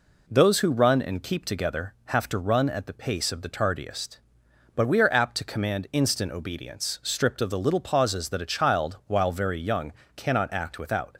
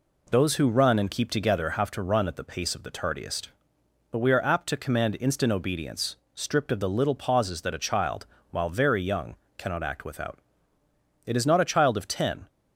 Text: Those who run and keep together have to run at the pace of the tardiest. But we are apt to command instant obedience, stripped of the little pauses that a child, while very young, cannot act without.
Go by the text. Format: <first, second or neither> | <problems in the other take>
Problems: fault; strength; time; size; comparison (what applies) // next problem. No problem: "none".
first | goes on to say "It is not a child of ten"; noticeable; from 11.2 s on; 1.2 s long